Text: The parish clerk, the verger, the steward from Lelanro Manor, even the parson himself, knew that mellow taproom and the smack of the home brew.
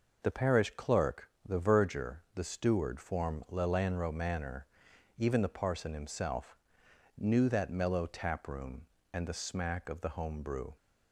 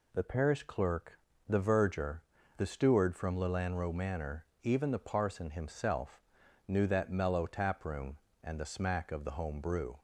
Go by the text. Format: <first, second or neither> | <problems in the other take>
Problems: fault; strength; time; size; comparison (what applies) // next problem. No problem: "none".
second | says "form" for "from"; at 2.9 s